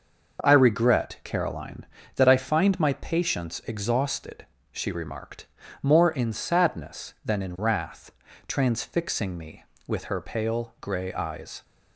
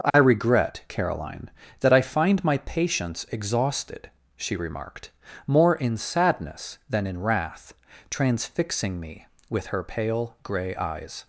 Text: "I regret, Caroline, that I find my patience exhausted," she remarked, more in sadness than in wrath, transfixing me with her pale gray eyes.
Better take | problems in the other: neither | none

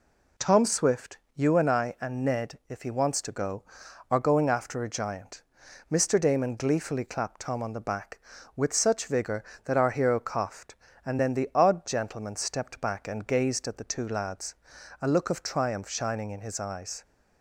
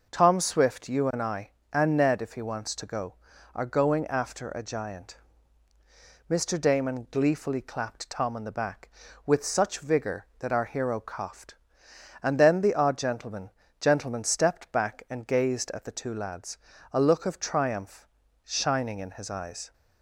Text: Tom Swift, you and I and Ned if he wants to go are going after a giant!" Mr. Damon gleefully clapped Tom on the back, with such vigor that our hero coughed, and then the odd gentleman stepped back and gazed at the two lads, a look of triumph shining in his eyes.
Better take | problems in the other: first | says "gentleman" twice; at 13.8 s // pauses between "triumph" and "shining"; at 18.0 s; 0.38 s long

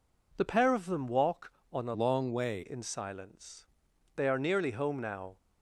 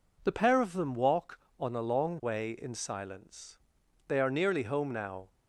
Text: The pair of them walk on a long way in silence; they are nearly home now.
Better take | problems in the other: second | changes voice from "long" to "way"; from 1.9 to 2.6 s; 0.7 s long

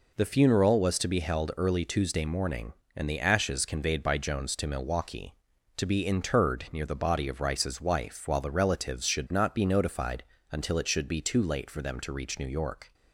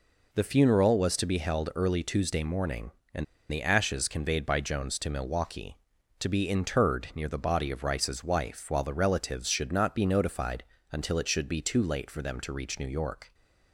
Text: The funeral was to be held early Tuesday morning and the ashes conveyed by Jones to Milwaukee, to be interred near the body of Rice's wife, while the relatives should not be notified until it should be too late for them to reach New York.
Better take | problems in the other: first | pauses between "and" and "the"; slight; at 3.2 s; 0.26 s long // pauses between "notified" and "until"; slight; at 10.6 s; 0.26 s long; slight in the first

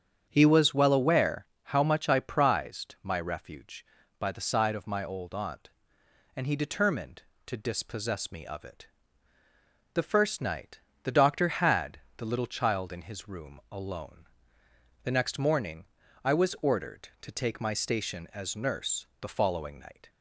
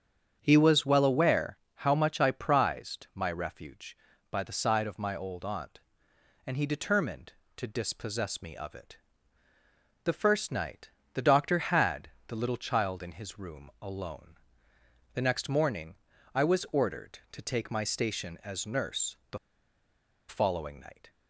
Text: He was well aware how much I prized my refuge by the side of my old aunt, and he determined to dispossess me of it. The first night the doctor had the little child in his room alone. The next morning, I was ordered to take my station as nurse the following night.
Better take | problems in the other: first | starts louder than the rest; strong; until 1.4 s; 8 dB; strong in the first // pauses between "aware" and "how"; slight; at 1.5 s; 0.18 s long; slight in the first // pauses between "night" and "the"; slight; at 10.9 s; 0.22 s long; slight in the first // pauses between "had" and "the"; slight; at 12.0 s; 0.18 s long; slight in the first // pauses between "the" and "following"; noticeable; at 19.3 s; 0.91 s long

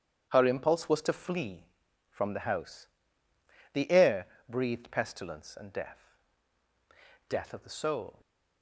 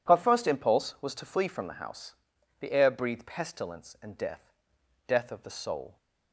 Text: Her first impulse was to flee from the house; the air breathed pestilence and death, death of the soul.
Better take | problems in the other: second | starts louder than the rest; strong; until 1.3 s; 9 dB // skips "first"; at 0.4 s // pauses between "air" and "breathed"; slight; at 4.2 s; 0.20 s long

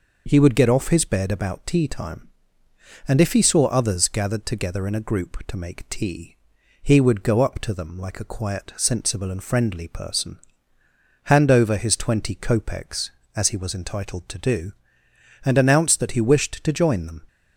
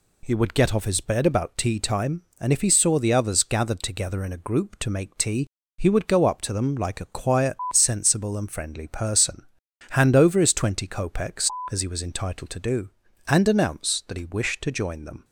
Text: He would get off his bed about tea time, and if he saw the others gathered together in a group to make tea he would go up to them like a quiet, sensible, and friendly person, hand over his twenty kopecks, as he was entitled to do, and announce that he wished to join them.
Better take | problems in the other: second | skips "the"; at 3.6 s // pauses between "tea" and "he"; noticeable; at 6.3 s; 0.48 s long; slight in the second

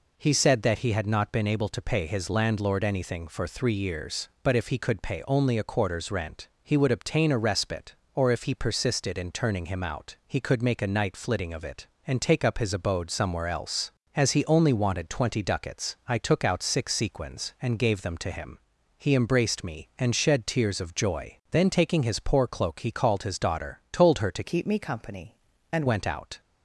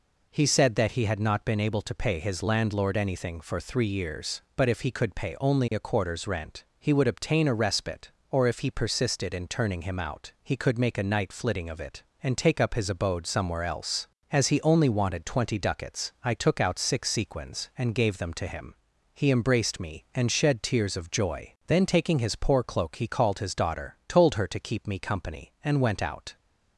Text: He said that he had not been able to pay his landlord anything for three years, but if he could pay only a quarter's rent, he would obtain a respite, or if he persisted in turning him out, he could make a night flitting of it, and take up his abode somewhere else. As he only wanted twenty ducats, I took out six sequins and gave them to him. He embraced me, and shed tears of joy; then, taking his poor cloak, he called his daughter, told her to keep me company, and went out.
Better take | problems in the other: second | changes voice from "keep" to "and"; from 24.4 to 25.8 s; 1.4 s long

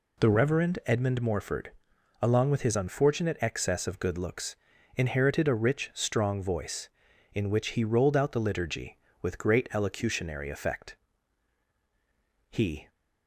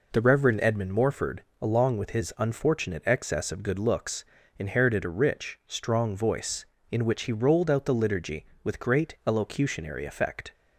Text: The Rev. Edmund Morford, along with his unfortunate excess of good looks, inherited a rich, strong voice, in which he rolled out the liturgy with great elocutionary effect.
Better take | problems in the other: second | goes on to say "He"; slight; from 12.5 s on; 0.38 s long

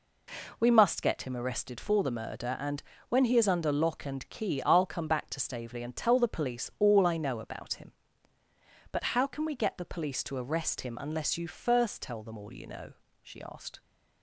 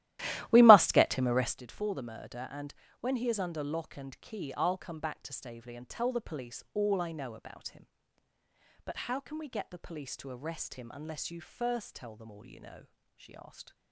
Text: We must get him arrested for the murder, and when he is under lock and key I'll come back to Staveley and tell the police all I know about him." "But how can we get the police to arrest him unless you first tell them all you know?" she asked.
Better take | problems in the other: first | starts louder than the rest; strong; until 1.6 s; 15 dB // pauses between "and" and "when"; slight; at 2.7 s; 0.26 s long; slight in the first

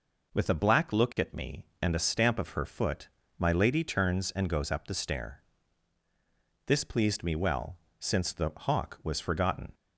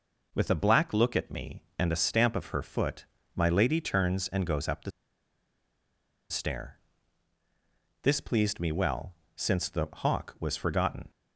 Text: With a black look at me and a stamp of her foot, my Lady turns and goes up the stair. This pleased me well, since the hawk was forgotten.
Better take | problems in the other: first | pauses between "the" and "stair"; strong; at 4.9 s; 1.3 s long

